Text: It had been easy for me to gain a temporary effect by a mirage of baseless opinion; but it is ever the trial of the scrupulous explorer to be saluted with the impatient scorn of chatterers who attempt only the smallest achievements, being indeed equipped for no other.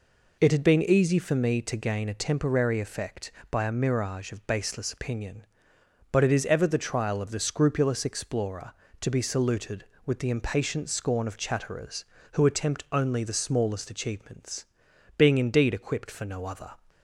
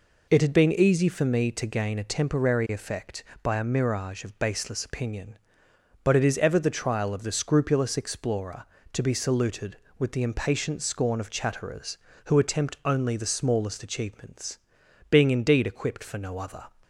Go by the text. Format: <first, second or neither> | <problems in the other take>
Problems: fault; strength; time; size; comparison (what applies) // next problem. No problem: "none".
neither | none